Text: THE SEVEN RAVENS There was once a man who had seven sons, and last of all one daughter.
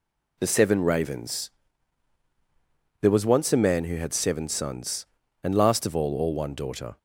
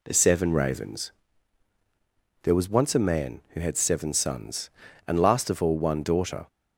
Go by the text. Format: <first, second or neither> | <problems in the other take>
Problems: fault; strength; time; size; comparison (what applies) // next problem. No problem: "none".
second | pauses between "RAVENS" and "There"; strong; at 1.4 s; 1.5 s long; strong in the second // says "all" twice; at 6.1 s